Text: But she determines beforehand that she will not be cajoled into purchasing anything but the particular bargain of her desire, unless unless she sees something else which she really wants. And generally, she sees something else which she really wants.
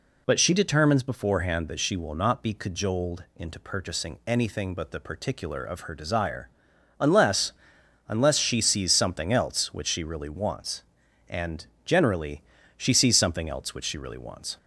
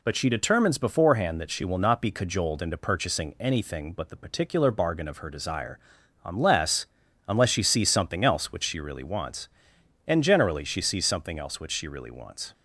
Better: second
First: skips "bargain"; at 5.6 s // pauses between "unless" and "unless"; noticeable; at 7.5 s; 0.56 s long // pauses between "And" and "generally"; slight; at 11.6 s; 0.20 s long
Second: pauses between "unless" and "unless"; at 6.8 s; 0.42 s long

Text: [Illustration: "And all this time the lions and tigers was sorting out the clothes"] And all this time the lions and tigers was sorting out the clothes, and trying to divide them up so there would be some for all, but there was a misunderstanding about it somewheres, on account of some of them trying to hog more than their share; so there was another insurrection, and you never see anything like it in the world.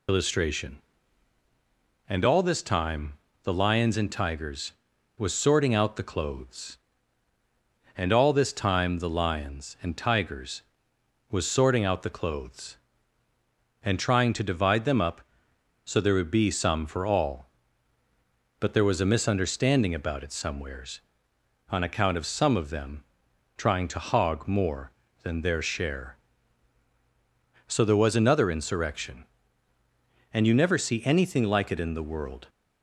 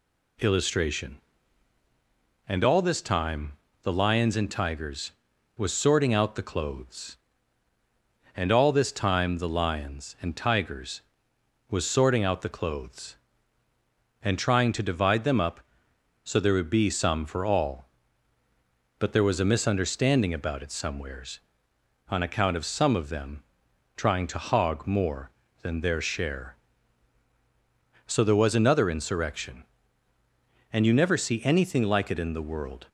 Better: second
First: loses the start of "Illustration"; at 0.0 s; 90 ms // pauses between "time" and "the"; slight; at 3.1 s; 0.30 s long // pauses between "them" and "trying"; noticeable; at 23.0 s; 0.52 s long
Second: pauses between "time" and "the"; slight; at 3.5 s; 0.30 s long // pauses between "them" and "trying"; noticeable; at 23.4 s; 0.52 s long

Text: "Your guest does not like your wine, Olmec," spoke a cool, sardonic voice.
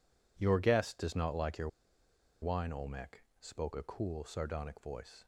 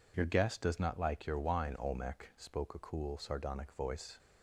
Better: second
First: pauses between "your" and "wine"; noticeable; at 1.6 s; 0.74 s long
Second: none

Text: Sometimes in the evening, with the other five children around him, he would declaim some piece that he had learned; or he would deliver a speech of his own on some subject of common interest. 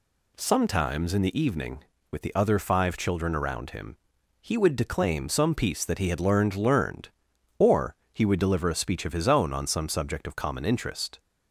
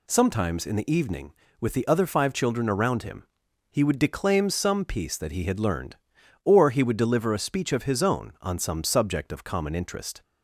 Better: second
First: says "learned" twice; at 6.5 s // pauses between "or" and "he"; slight; at 7.9 s; 0.20 s long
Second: none

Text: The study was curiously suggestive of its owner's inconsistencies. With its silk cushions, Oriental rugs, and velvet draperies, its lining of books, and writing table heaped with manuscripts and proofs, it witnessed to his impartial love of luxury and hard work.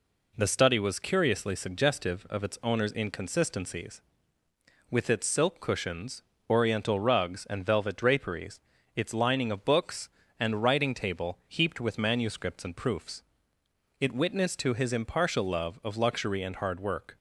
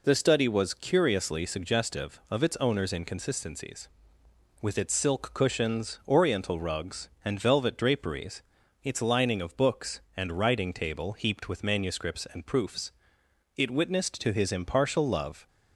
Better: first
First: none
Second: stops before "of luxury and hard work"; at 15.4 s

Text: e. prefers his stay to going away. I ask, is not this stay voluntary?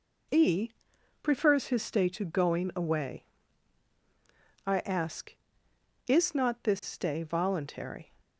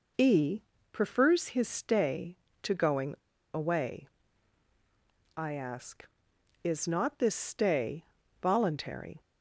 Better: first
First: none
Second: pauses between "going" and "away"; at 3.1 s; 0.37 s long // pauses between "stay" and "voluntary"; slight; at 8.0 s; 0.36 s long

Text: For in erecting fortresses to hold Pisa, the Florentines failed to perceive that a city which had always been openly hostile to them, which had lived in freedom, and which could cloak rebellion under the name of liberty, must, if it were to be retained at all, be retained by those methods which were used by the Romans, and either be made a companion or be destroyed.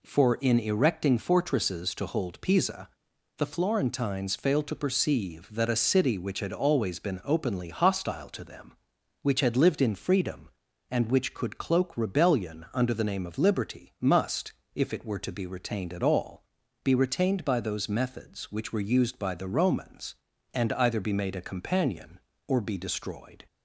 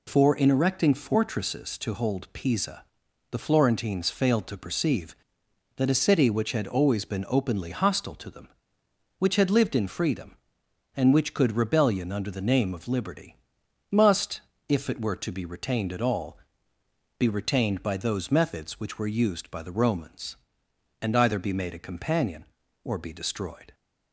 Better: first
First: none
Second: skips "cloak"; at 11.5 s

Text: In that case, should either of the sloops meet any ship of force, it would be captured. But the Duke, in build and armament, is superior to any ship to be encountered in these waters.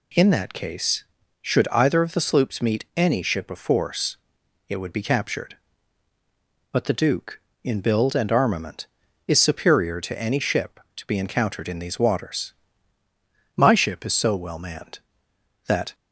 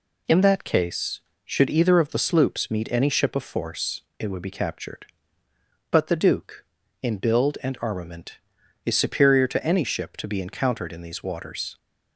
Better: second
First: goes on to say "My ship is so well manned that"; strong; from 13.5 s on; 2.3 s long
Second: none

